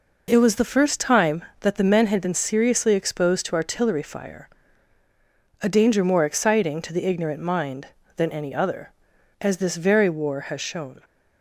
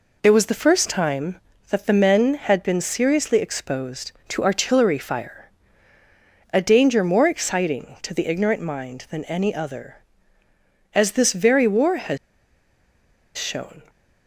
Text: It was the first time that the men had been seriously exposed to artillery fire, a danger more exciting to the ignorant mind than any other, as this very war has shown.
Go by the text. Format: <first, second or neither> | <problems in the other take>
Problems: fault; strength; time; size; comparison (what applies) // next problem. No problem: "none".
first | pauses between "has" and "shown"; at 12.1 s; 1.1 s long